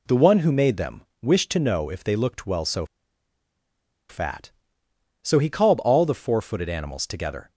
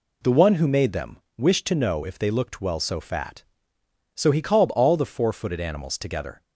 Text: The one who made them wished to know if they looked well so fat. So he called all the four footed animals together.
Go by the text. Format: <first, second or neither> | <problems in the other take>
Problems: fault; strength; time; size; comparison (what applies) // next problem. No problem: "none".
second | pauses between "them" and "wished"; slight; at 1.0 s; 0.18 s long; slight in the second // pauses between "so" and "fat"; strong; at 2.8 s; 1.2 s long